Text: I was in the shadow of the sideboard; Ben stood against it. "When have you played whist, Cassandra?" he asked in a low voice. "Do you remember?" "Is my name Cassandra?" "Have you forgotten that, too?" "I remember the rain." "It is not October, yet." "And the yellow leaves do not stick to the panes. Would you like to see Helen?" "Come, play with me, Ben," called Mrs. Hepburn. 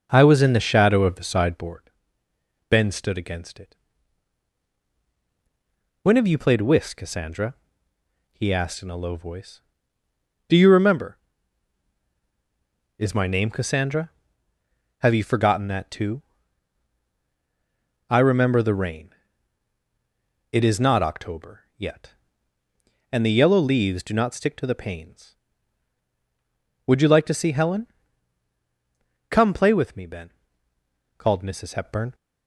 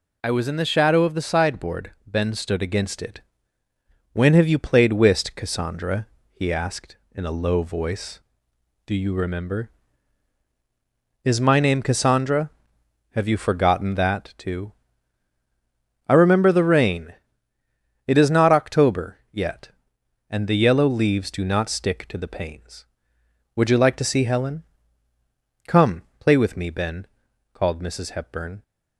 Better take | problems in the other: second | starts louder than the rest; noticeable; until 1.2 s; 5.5 dB

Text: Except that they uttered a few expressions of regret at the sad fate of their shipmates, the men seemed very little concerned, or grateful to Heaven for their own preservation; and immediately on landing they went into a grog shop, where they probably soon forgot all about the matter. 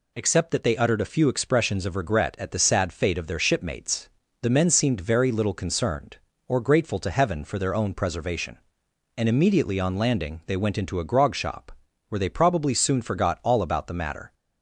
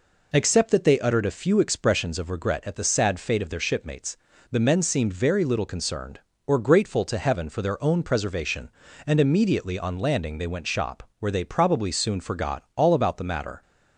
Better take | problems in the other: first | skips "into a grog"; at 10.6 s

